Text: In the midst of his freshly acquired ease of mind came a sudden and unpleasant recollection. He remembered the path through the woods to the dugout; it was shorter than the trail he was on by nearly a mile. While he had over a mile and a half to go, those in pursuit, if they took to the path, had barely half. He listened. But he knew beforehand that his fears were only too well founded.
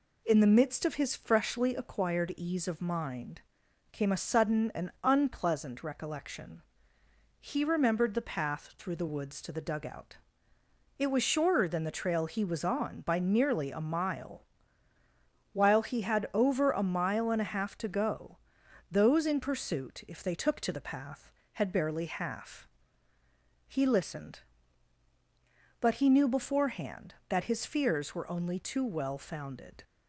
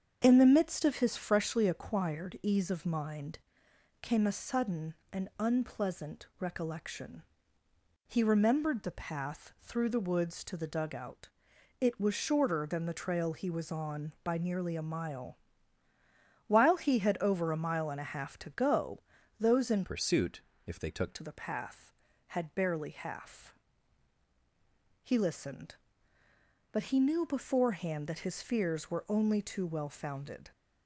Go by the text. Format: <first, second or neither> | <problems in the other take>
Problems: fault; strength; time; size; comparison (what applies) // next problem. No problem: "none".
first | starts louder than the rest; strong; until 1.2 s; 7.5 dB // pauses between "mind" and "came"; noticeable; at 3.3 s; 0.62 s long; noticeable in the first // changes voice from "pursuit" to "took"; from 19.8 to 21.1 s; 1.3 s long